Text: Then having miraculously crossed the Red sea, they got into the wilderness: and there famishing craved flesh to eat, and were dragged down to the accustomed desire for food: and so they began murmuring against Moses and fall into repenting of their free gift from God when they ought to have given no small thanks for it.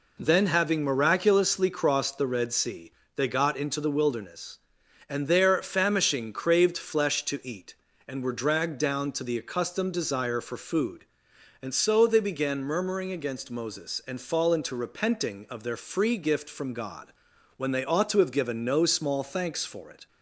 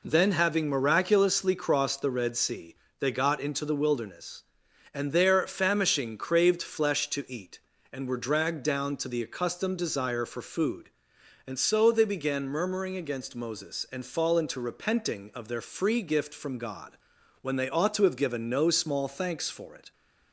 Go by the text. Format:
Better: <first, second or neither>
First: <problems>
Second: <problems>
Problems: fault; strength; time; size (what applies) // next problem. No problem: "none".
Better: neither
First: pauses between "God" and "when"; noticeable; at 17.1 s; 0.46 s long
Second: pauses between "God" and "when"; noticeable; at 16.9 s; 0.46 s long